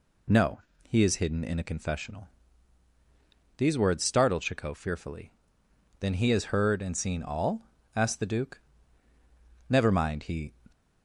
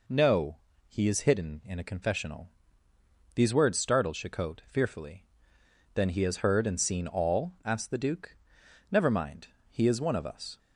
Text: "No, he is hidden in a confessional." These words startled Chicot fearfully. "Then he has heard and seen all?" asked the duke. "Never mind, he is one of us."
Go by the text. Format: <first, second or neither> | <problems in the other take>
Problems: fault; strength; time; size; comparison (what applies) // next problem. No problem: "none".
second | stops before "is one of us"; at 10.7 s